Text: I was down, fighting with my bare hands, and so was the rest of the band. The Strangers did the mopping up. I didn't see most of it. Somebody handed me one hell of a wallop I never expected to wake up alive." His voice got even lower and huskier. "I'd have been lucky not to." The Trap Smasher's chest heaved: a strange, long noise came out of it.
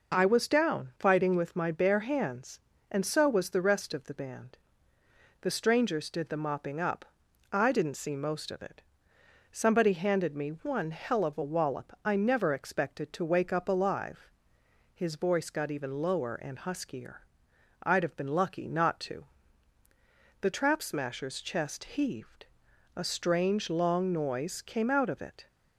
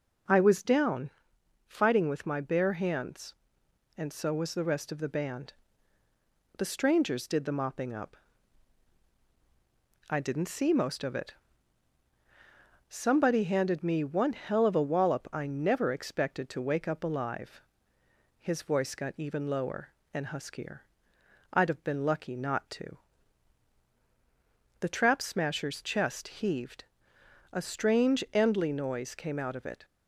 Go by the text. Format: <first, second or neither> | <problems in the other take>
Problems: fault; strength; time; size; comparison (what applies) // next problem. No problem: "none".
first | says "endly" for "long"; at 28.3 s